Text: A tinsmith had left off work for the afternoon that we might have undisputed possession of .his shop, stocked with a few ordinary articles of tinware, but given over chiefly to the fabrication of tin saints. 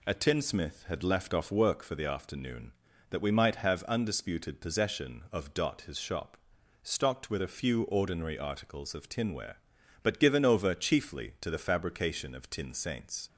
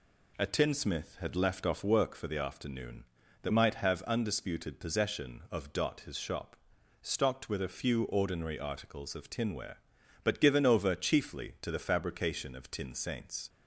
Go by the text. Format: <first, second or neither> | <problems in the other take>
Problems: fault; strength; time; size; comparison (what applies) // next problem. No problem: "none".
first | skips "we"; at 3.5 s